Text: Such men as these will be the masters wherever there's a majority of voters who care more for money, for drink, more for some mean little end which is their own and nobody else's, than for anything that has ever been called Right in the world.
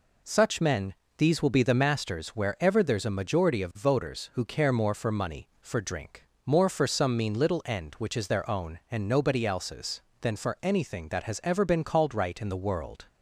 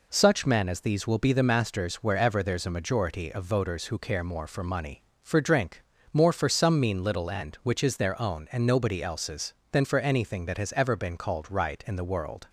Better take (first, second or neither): second